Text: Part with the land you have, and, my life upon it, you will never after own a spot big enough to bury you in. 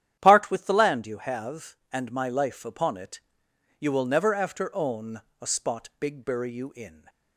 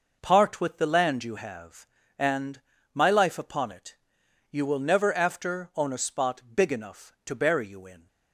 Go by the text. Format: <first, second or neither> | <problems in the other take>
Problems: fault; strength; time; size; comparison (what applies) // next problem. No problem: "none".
second | starts louder than the rest; strong; until 1.2 s; 10.5 dB // pauses between "own" and "a"; slight; at 5.2 s; 0.20 s long // skips "enough to"; at 6.2 s